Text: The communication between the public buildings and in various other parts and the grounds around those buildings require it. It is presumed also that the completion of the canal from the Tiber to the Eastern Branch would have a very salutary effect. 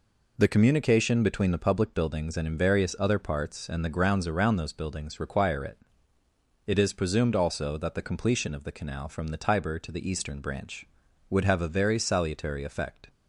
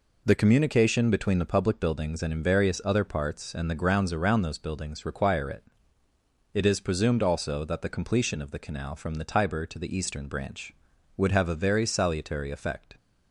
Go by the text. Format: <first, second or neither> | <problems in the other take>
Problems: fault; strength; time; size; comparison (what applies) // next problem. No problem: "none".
neither | none